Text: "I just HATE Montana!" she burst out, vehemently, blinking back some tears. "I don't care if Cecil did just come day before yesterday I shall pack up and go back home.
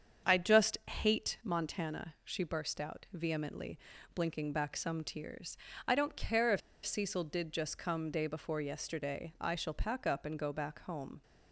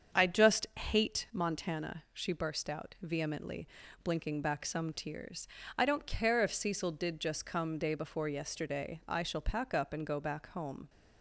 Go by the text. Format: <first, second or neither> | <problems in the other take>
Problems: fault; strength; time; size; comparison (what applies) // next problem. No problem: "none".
second | starts louder than the rest; strong; until 1.3 s; 7.5 dB; strong in the second // pauses between "if" and "Cecil"; slight; at 6.6 s; 0.25 s long